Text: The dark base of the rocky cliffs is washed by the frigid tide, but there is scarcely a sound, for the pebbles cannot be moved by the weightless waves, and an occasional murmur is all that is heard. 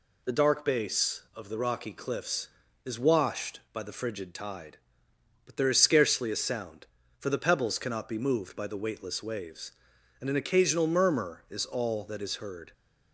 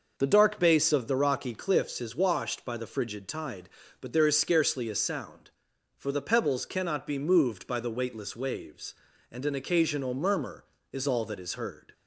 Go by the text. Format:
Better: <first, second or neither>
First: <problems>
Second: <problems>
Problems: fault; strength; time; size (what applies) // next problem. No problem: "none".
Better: neither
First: none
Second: none